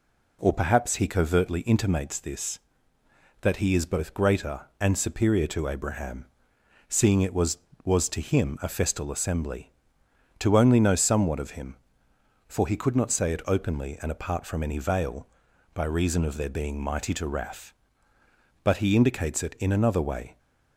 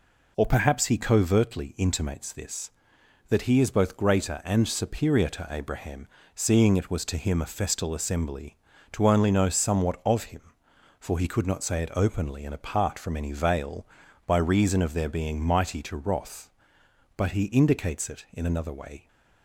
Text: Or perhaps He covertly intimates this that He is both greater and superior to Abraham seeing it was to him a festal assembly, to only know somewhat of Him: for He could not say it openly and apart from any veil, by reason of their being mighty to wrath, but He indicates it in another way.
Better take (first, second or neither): second